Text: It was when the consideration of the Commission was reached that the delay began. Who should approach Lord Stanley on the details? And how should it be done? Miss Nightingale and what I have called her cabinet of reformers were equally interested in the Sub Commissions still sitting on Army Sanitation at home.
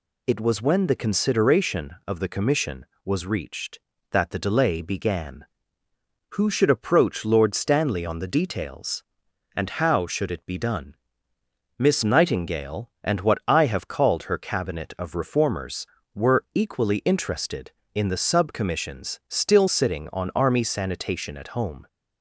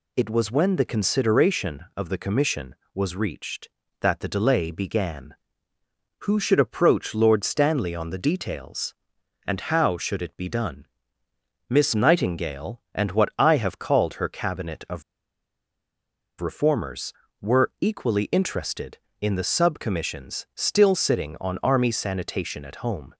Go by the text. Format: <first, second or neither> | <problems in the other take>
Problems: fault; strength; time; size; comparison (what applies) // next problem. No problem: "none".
first | pauses between "of" and "reformers"; strong; at 15.0 s; 1.3 s long